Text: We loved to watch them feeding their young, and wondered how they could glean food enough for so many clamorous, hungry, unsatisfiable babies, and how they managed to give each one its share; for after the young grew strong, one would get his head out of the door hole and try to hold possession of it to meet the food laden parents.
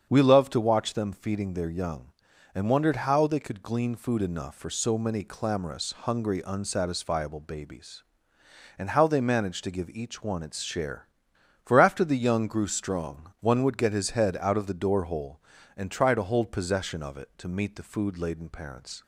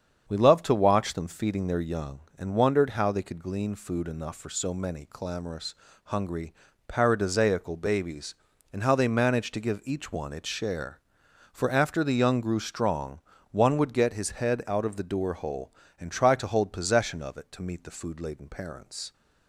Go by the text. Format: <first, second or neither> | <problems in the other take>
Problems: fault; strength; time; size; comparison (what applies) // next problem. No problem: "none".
first | starts louder than the rest; strong; until 1.2 s; 7.5 dB; strong in the first // says "paradisaical" for "unsatisfiable"; at 6.8 s